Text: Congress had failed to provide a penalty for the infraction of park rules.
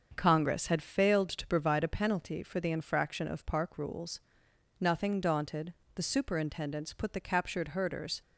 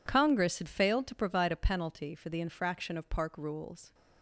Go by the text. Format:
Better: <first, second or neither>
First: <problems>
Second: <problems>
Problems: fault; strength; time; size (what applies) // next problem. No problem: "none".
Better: second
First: starts louder than the rest; until 1.1 s; 7 dB // goes on to say "Nothing daunted the superintendents put the captured herders"; strong; from 4.7 s on; 3.4 s long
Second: none